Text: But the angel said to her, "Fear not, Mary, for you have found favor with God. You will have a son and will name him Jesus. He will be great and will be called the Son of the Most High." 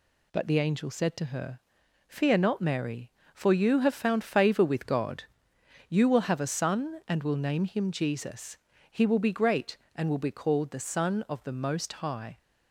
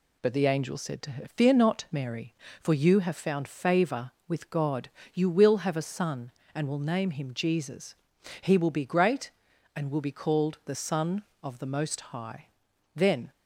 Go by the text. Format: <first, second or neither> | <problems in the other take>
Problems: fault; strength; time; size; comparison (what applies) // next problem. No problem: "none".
first | goes on to say "Then"; slight; from 12.9 s on; 0.36 s long